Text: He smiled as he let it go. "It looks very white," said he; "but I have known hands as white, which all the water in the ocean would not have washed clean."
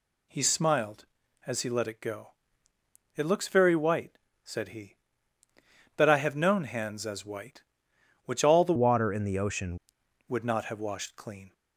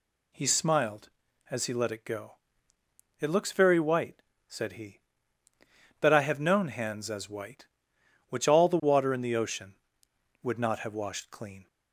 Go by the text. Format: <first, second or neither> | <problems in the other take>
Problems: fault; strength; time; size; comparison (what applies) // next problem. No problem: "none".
second | changes voice from "water" to "ocean"; from 8.7 to 9.7 s; 1.0 s long